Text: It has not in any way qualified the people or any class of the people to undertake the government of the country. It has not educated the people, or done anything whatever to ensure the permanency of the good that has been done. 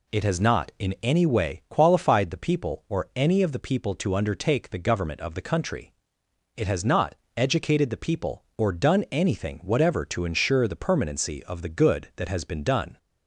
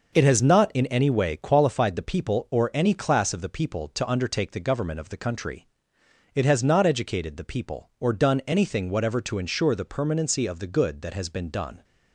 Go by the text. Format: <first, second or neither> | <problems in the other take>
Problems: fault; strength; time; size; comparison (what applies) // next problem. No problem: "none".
second | skips "class"; at 3.4 s // pauses between "not" and "educated"; slight; at 7.1 s; 0.20 s long